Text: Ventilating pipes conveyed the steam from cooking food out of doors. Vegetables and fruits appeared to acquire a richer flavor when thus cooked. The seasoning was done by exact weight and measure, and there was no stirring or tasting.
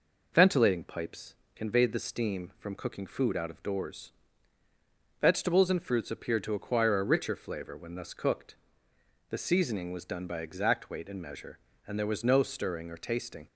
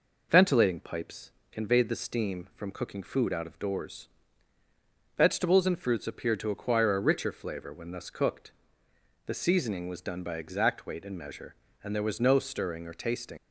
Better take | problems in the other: first | pauses between "pipes" and "conveyed"; slight; at 1.3 s; 0.20 s long; slight in the first // leaves "tasting" unfinished; at 13.3 s; 55 ms

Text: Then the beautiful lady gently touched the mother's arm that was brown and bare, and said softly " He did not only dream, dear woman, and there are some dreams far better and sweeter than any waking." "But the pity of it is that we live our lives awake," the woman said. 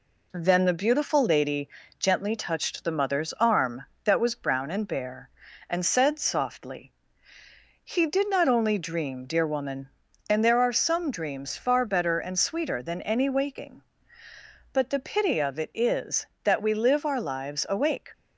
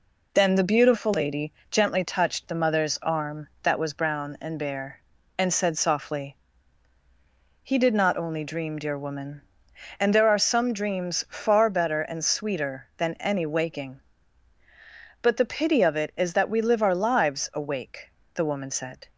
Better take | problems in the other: second | pauses between "lady" and "gently"; slight; at 1.6 s; 0.30 s long; slight in the second // stops before "the woman said"; at 18.1 s

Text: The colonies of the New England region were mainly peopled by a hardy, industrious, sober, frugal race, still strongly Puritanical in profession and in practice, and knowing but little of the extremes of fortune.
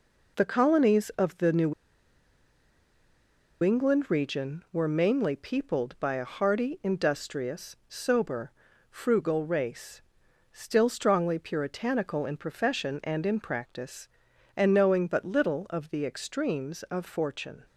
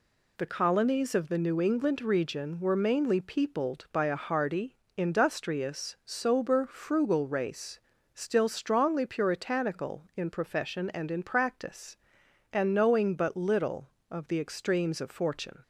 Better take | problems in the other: second | pauses between "New" and "England"; strong; at 1.7 s; 1.9 s long

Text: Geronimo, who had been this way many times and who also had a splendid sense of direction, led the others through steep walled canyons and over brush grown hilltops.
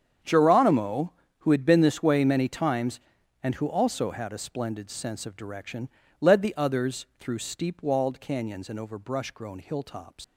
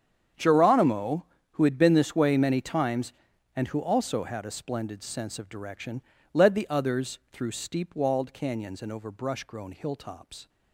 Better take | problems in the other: second | starts louder than the rest; strong; until 1.5 s; 8 dB; strong in the second // leaves "hilltops" unfinished; at 10.2 s; 110 ms

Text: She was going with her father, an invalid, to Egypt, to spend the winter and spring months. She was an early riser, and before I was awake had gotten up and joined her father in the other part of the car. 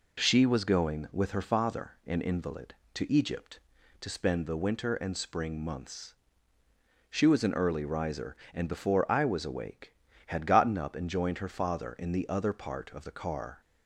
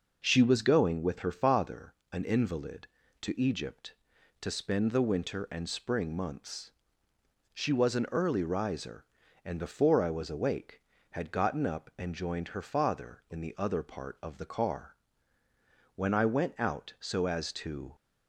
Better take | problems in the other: first | goes on to say "When I went out so as to"; strong; from 15.9 s on; 1.9 s long

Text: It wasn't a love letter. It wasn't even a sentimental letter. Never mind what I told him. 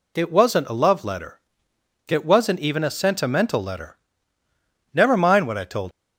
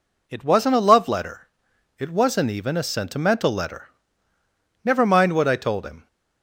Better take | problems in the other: second | stops before "him"; at 5.9 s

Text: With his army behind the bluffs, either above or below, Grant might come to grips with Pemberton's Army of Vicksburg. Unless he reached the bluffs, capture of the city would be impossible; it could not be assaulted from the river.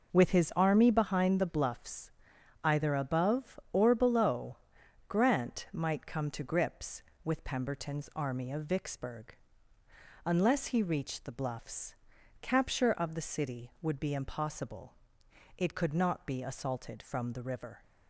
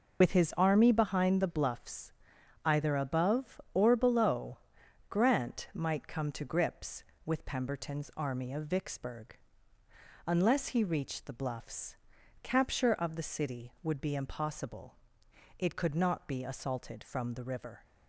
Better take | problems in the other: first | loses the start of "With"; at 0.2 s; 75 ms

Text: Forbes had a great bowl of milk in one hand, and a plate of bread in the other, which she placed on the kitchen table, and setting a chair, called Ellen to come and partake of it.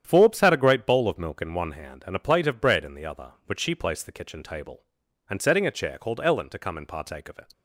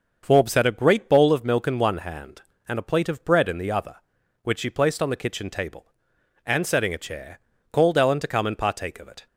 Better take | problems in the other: second | starts louder than the rest; strong; until 1.0 s; 9.5 dB; also in the second // skips "on"; at 4.0 s

